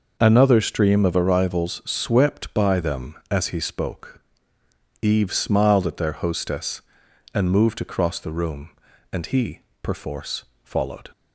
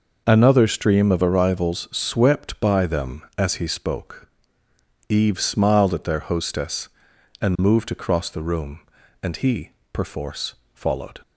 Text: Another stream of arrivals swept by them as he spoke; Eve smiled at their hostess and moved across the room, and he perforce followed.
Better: neither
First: pauses between "he" and "perforce"; slight; at 9.6 s; 0.20 s long // pauses between "perforce" and "followed"; slight; at 10.4 s; 0.20 s long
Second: pauses between "he" and "perforce"; slight; at 9.7 s; 0.20 s long // pauses between "perforce" and "followed"; slight; at 10.5 s; 0.20 s long

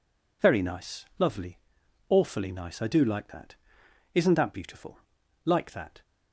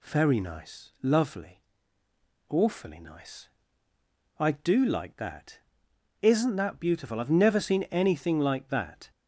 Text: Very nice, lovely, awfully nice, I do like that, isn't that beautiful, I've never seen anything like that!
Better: second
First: skips "I've never seen anything"; at 5.2 s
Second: none

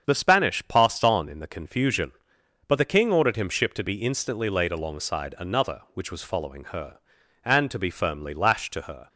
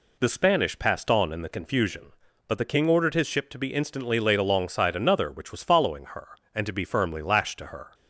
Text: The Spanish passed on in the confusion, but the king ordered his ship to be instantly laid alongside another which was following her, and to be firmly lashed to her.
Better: second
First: starts louder than the rest; strong; until 1.0 s; 7.5 dB // says "him" for "his"; at 3.3 s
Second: none

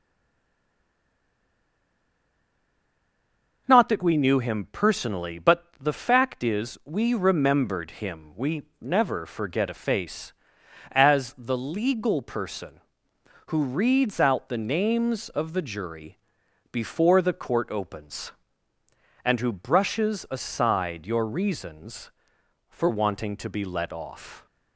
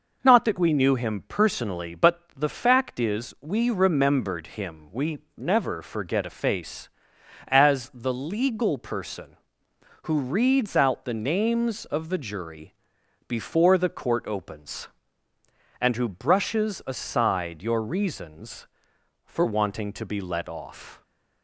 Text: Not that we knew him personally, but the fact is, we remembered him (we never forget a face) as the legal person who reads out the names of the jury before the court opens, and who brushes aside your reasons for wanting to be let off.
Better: second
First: stays silent before the first word; strong; until 3.6 s; 3.6 s long // pauses between "but" and "the"; slight; at 5.6 s; 0.16 s long // pauses between "jury" and "before"; noticeable; at 16.1 s; 0.54 s long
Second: pauses between "but" and "the"; slight; at 2.1 s; 0.16 s long // pauses between "jury" and "before"; noticeable; at 12.7 s; 0.54 s long

